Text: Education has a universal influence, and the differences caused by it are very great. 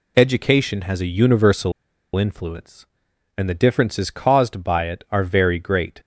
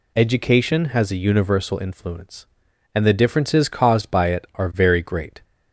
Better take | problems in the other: second | pauses between "universal" and "influence"; at 1.7 s; 0.43 s long

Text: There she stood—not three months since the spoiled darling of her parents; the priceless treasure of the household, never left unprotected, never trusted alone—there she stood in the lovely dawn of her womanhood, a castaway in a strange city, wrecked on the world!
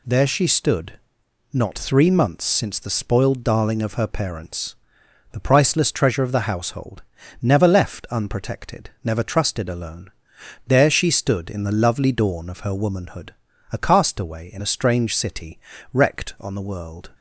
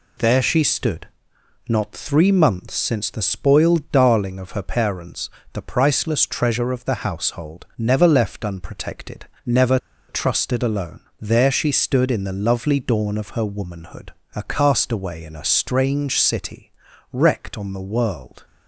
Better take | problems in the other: first | pauses between "never" and "trusted"; slight; at 9.7 s; 0.31 s long

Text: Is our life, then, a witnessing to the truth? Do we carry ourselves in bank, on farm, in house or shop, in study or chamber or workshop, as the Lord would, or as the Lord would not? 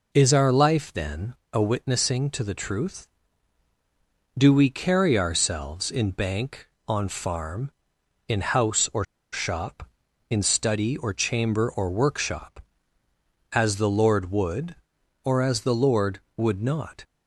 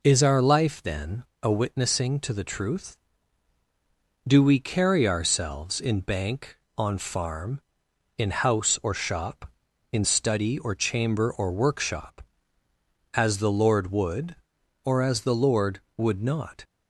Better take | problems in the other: second | pauses between "or" and "shop"; slight; at 9.0 s; 0.28 s long

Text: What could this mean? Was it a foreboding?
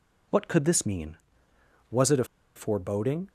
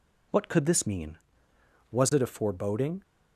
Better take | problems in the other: second | pauses between "a" and "foreboding"; slight; at 2.2 s; 0.31 s long

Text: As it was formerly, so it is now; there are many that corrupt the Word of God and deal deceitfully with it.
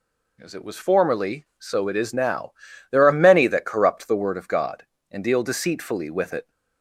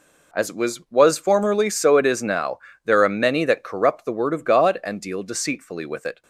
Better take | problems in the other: first | says "was" twice; at 0.9 s

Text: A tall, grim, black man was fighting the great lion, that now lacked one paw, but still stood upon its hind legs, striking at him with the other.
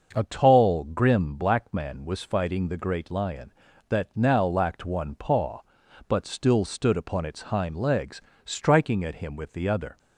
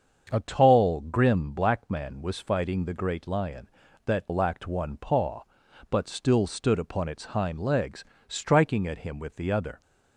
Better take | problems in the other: first | starts louder than the rest; until 1.3 s; 7 dB; also in the first // skips "now"; at 4.2 s

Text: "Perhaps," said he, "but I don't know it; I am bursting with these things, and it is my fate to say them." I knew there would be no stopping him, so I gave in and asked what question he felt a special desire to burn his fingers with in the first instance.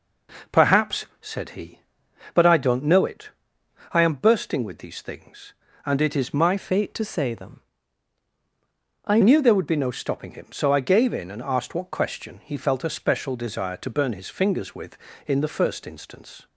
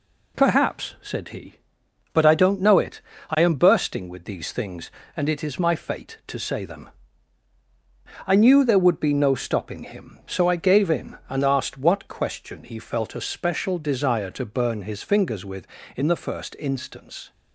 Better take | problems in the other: second | changes voice from "fate" to "I"; from 6.5 to 9.2 s; 2.7 s long

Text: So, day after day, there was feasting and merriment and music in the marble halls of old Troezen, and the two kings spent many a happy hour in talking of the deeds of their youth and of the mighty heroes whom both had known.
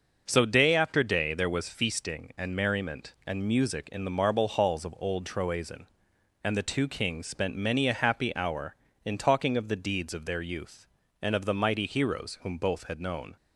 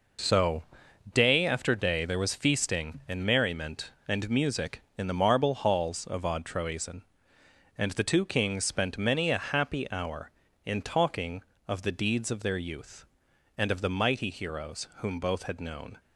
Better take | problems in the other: first | says "odd" for "old"; at 6.2 s

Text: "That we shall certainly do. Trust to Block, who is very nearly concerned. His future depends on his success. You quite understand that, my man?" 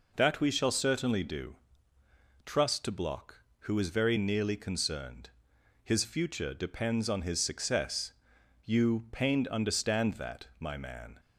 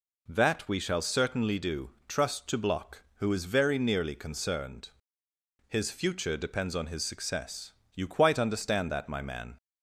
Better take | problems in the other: second | says "pained" for "quite"; at 9.1 s

